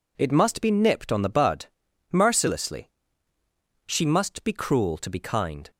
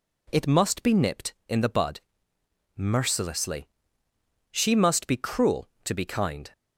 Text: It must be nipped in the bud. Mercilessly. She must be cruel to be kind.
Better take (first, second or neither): second